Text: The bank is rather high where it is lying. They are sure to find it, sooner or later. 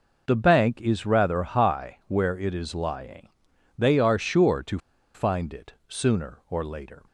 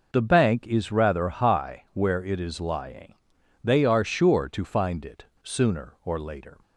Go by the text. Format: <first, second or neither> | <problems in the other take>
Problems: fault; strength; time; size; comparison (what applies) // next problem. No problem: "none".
second | pauses between "to" and "find"; at 4.7 s; 0.36 s long